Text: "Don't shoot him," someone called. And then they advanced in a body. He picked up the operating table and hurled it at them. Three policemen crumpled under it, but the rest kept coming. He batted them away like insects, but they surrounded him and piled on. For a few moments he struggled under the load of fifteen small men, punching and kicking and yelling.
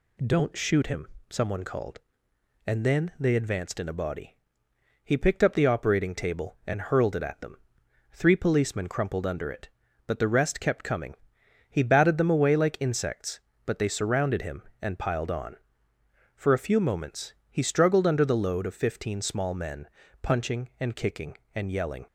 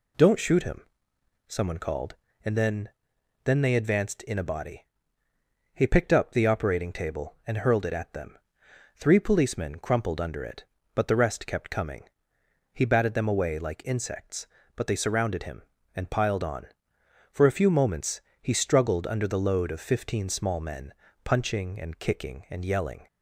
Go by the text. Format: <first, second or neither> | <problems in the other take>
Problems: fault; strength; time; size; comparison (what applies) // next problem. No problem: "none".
first | says "then" twice; at 3.4 s // pauses between "moments" and "he"; slight; at 18.2 s; 0.20 s long; slight in the first